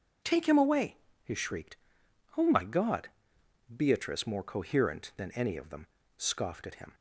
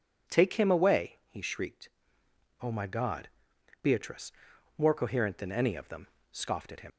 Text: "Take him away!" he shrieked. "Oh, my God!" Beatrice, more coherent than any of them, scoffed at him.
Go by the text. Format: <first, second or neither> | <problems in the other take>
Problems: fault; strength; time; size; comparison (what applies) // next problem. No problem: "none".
first | leaves "him" unfinished; at 6.9 s; 70 ms